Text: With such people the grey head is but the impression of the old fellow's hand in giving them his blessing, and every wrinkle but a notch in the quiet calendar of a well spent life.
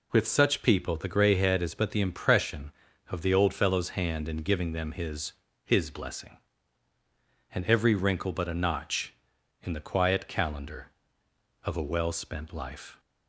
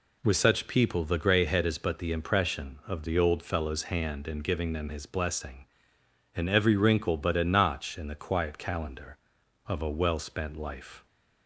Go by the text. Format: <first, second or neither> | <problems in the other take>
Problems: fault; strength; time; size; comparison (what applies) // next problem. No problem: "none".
second | says "his" twice; at 5.6 s